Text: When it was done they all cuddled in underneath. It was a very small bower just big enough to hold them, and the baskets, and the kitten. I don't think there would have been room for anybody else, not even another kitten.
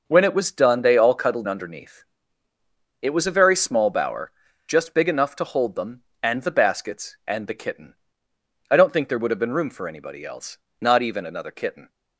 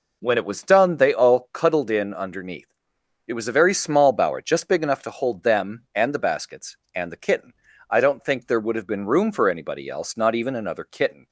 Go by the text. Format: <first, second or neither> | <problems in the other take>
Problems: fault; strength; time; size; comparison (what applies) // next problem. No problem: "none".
second | starts louder than the rest; noticeable; until 1.0 s; 6 dB // skips "in"; at 1.4 s // pauses between "bower" and "just"; slight; at 4.3 s; 0.34 s long